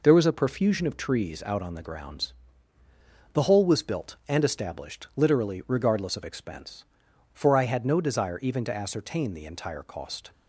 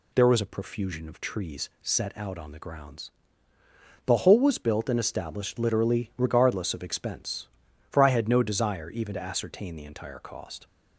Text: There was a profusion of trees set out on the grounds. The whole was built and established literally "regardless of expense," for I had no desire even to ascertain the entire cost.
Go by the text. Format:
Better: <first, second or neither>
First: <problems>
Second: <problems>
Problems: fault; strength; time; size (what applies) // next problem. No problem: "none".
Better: second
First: skips "set"; at 1.4 s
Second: none